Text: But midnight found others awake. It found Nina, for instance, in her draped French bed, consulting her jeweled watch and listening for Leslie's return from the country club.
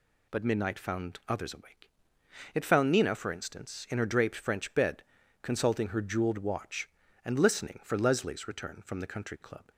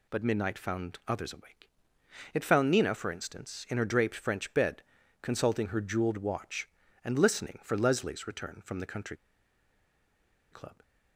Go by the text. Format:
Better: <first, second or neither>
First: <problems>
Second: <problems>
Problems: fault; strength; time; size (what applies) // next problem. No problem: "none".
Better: first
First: none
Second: pauses between "country" and "club"; strong; at 9.1 s; 1.3 s long